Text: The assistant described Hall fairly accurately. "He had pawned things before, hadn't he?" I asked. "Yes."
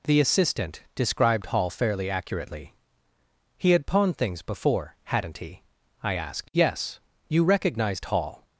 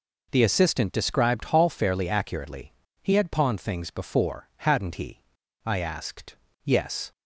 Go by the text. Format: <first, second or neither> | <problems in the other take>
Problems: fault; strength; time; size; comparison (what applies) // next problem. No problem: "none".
second | goes on to say "You recognized Hall"; noticeable; from 7.2 s on; 1.1 s long